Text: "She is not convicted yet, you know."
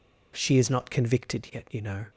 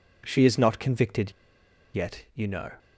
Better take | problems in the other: first | pauses between "convicted" and "yet"; noticeable; at 1.3 s; 0.64 s long

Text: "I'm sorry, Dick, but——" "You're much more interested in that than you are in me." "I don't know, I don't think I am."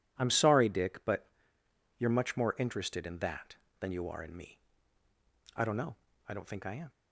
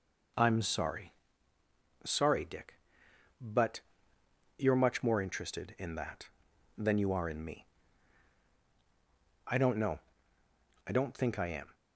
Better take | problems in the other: first | says "sorry" twice; at 2.0 s

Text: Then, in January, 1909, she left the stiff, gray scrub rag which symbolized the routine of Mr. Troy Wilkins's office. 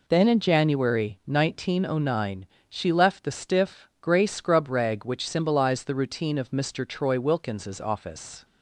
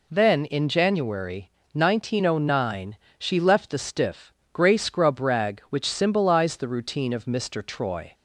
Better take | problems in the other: first | stops before "Wilkins's office"; at 8.1 s

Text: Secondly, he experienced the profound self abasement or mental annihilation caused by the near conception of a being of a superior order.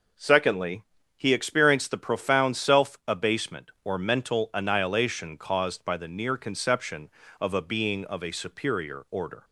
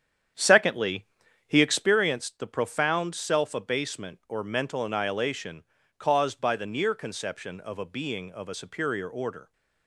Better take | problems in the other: first | starts louder than the rest; strong; until 2.0 s; 9 dB // pauses between "annihilation" and "caused"; slight; at 5.6 s; 0.36 s long

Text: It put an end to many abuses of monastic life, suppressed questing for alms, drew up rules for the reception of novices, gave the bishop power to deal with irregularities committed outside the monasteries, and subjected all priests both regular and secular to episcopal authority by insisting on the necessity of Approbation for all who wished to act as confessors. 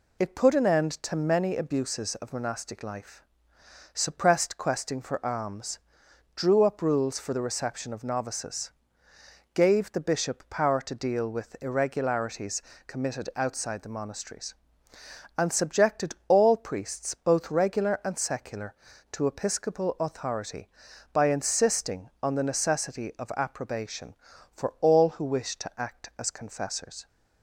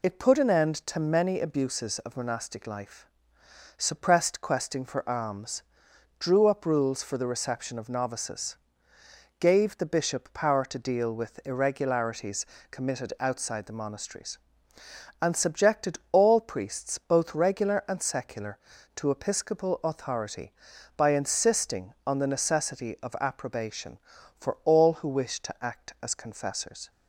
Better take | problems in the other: neither | pauses between "irregularities" and "committed"; slight; the same in both

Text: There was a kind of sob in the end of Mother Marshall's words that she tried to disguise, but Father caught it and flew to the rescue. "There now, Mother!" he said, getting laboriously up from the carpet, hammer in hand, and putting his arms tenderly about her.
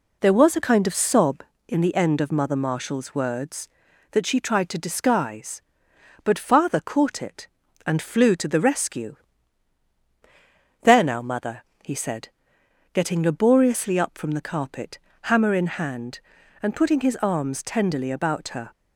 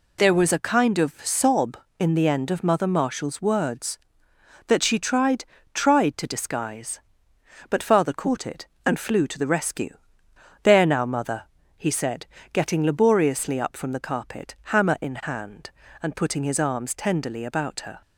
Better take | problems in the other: first | says "tried" twice; at 5.7 s

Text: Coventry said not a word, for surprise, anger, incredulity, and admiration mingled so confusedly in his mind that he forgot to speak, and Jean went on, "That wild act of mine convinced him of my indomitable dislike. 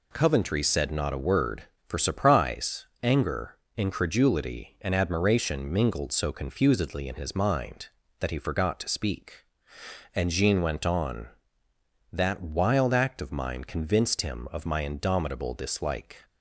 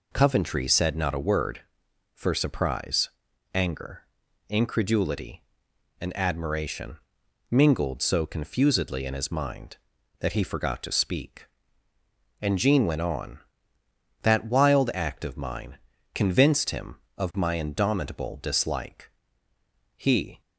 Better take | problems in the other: first | pauses between "admiration" and "mingled"; noticeable; at 6.9 s; 0.52 s long // pauses between "mine" and "convinced"; slight; at 15.7 s; 0.36 s long // goes on to say "He"; slight; from 19.9 s on; 0.44 s long

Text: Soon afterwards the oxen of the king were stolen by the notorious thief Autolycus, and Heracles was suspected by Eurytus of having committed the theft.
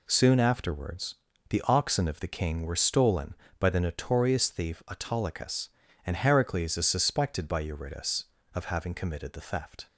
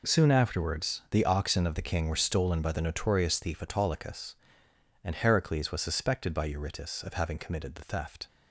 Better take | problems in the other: second | pauses between "afterwards" and "the"; slight; at 1.1 s; 0.32 s long // says "is" for "was"; at 6.7 s

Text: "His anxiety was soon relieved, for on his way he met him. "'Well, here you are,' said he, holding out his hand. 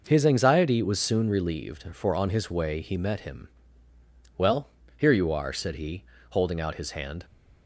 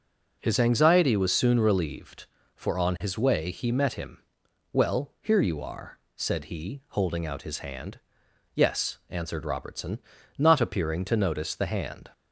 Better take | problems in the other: first | goes on to say "Yes answered Robertson not appearing to notice the hand"; strong; from 8.5 s on; 3.5 s long

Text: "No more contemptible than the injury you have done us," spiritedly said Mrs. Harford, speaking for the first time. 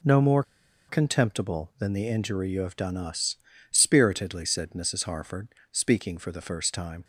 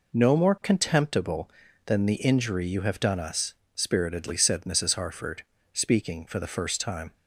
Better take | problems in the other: second | pauses between "more" and "contemptible"; noticeable; at 0.4 s; 0.46 s long

